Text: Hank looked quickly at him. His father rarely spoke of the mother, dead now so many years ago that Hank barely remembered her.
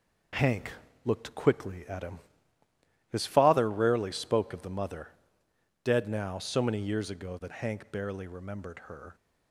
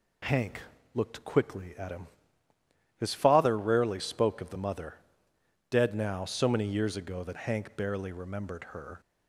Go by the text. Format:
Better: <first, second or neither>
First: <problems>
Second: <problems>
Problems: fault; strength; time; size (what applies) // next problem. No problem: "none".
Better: second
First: gets quieter; noticeable; throughout; 5.5 dB // pauses between "Hank" and "looked"; slight; at 0.7 s; 0.32 s long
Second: pauses between "Hank" and "looked"; slight; at 0.6 s; 0.32 s long